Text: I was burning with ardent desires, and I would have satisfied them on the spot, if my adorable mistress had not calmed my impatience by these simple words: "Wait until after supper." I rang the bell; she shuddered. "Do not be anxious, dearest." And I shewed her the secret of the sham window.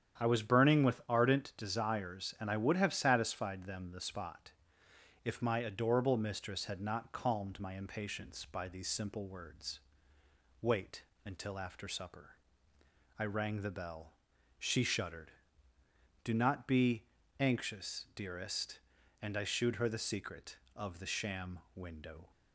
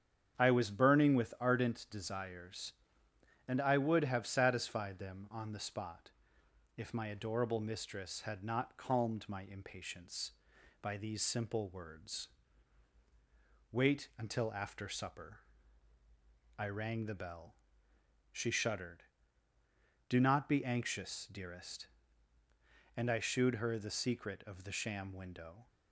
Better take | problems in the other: second | starts louder than the rest; strong; until 1.2 s; 9 dB; strong in the second // skips "on"; at 3.9 s // pauses between "Wait" and "until"; slight; at 11.0 s; 0.24 s long // pauses between "be" and "anxious"; slight; at 17.0 s; 0.34 s long // pauses between "sham" and "window"; slight; at 21.5 s; 0.16 s long

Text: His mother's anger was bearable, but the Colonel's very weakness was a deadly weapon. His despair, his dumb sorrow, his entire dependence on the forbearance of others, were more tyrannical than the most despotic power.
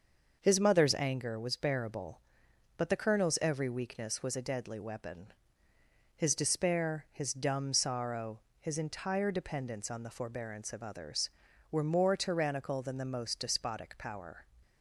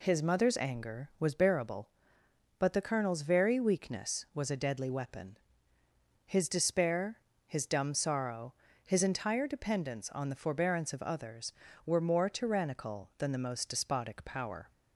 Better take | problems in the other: second | starts louder than the rest; until 1.4 s; 6 dB // says "every" for "very"; at 3.4 s

